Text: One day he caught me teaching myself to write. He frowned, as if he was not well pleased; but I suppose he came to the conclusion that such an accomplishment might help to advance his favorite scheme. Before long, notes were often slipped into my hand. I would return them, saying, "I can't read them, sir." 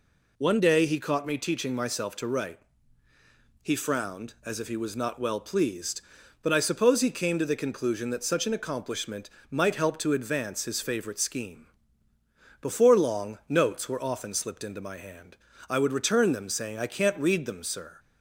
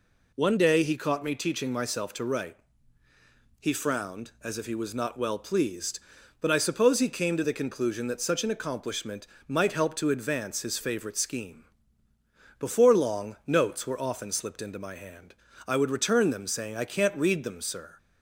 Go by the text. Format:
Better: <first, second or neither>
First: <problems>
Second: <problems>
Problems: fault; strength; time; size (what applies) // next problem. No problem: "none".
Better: neither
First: pauses between "accomplishment" and "might"; slight; at 9.3 s; 0.18 s long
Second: pauses between "accomplishment" and "might"; slight; at 9.2 s; 0.18 s long